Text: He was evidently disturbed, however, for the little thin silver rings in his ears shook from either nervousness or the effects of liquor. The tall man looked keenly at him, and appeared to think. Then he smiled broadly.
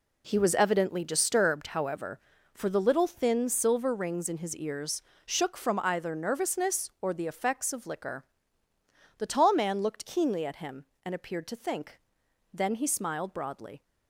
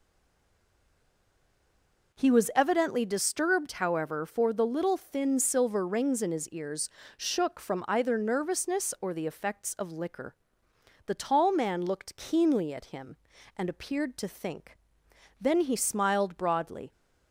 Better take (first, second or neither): first